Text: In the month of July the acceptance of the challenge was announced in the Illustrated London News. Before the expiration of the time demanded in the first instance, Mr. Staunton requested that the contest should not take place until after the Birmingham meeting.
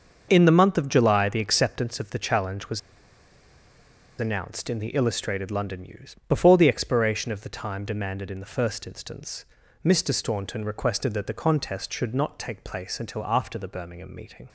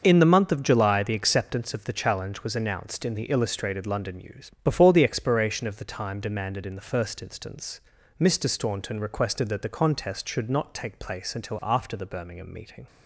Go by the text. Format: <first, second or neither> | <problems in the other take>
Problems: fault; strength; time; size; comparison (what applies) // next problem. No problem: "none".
second | starts louder than the rest; until 1.3 s; 6.5 dB; also in the second // pauses between "was" and "announced"; strong; at 2.7 s; 1.4 s long